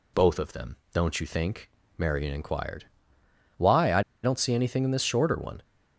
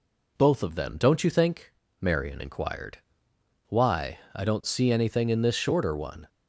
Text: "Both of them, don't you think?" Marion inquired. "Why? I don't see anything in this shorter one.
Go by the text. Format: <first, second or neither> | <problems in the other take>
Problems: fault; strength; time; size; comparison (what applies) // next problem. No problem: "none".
second | pauses between "I" and "don't"; slight; at 4.0 s; 0.22 s long